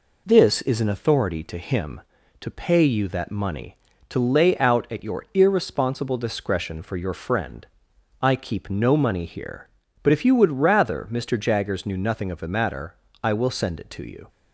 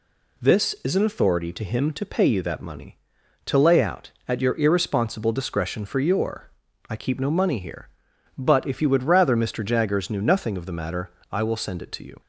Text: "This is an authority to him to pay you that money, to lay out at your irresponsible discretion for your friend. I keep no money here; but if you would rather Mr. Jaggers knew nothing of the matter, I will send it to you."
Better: first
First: none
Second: skips "friend"; at 6.7 s

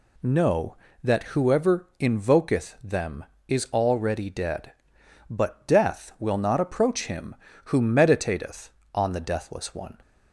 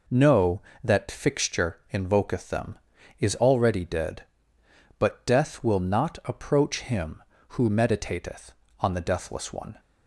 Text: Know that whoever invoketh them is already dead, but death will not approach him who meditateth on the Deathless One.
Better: first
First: none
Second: says "fixture" for "whoever"; at 1.0 s

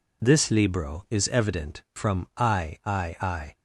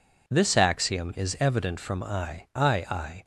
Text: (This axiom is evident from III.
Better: second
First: says "libro" for "axiom"; at 0.4 s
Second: none

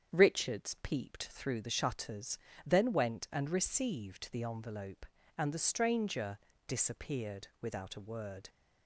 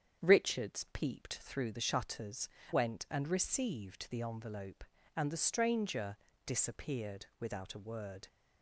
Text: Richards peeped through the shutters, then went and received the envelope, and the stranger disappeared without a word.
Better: first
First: starts louder than the rest; strong; until 1.2 s; 8 dB // pauses between "stranger" and "disappeared"; slight; at 6.3 s; 0.28 s long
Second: starts louder than the rest; strong; until 1.3 s; 8 dB // skips "then"; at 2.6 s // pauses between "stranger" and "disappeared"; slight; at 6.1 s; 0.28 s long

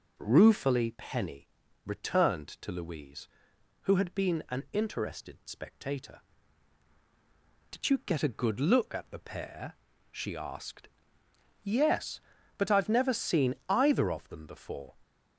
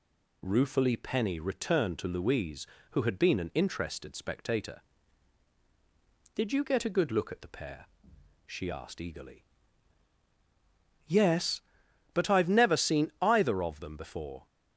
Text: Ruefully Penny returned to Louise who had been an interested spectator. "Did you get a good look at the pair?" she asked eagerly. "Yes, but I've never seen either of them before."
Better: second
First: pauses between "Penny" and "returned"; slight; at 1.4 s; 0.36 s long // skips "eagerly"; at 11.2 s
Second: none

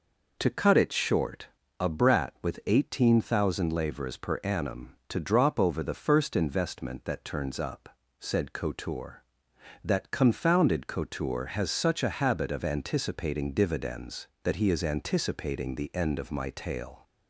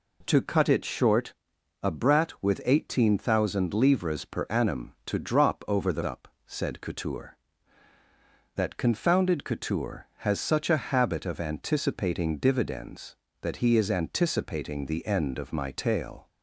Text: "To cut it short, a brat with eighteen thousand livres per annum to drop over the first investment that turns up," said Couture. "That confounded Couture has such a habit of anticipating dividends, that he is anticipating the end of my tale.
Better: first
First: none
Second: skips "first investment that turns"; at 6.0 s

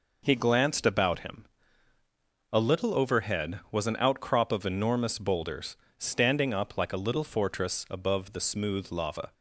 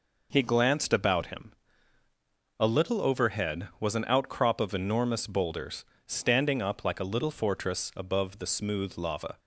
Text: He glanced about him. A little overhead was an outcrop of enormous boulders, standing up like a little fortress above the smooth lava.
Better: neither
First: none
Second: none

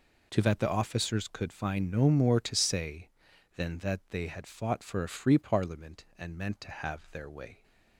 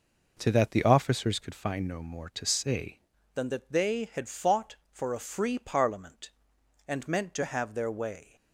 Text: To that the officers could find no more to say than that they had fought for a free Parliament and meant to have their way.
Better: first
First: none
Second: changes voice at "than"; from 3.3 s on; 5.0 s long

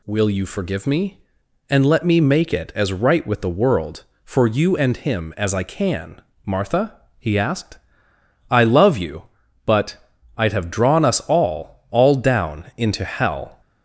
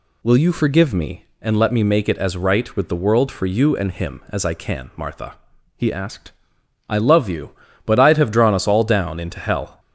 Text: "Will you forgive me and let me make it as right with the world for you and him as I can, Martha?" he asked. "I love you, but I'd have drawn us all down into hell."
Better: second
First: pauses between "but" and "I'd"; at 9.9 s; 0.42 s long // says "all" twice; at 11.9 s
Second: none

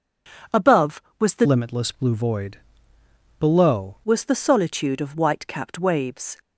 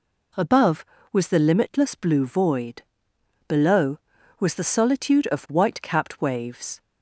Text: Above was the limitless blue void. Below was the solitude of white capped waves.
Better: second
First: changes voice from "limitless" to "Below"; from 1.4 to 3.9 s; 2.5 s long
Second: none

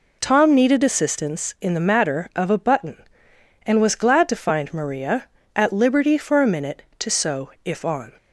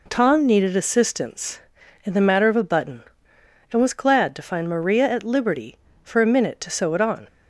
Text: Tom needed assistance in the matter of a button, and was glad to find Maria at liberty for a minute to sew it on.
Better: second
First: says "if" for "it"; at 7.6 s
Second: none

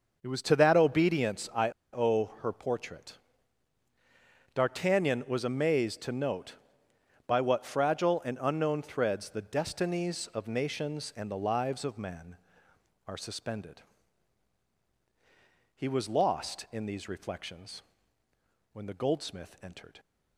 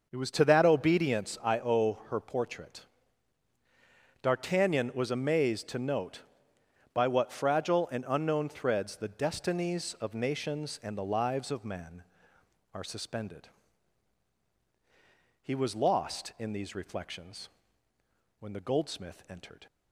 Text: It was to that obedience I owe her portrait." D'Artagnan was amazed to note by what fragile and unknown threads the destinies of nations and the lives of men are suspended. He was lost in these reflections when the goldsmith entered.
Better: second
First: starts louder than the rest; until 1.2 s; 6 dB // pauses between "I" and "owe"; slight; at 1.6 s; 0.23 s long // pauses between "reflections" and "when"; noticeable; at 17.8 s; 0.92 s long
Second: starts louder than the rest; until 1.1 s; 6 dB // pauses between "reflections" and "when"; noticeable; at 17.4 s; 0.92 s long

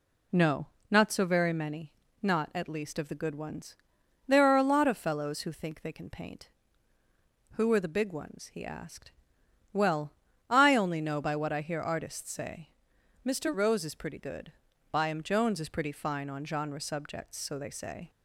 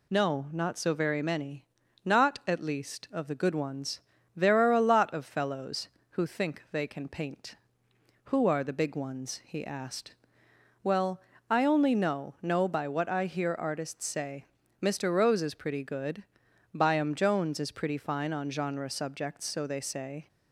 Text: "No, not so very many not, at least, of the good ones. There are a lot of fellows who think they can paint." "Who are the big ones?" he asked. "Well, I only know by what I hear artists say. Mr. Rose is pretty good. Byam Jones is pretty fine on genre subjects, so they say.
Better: first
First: pauses between "many" and "not"; slight; at 1.9 s; 0.28 s long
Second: pauses between "many" and "not"; at 1.6 s; 0.44 s long // says "know" twice; at 12.3 s

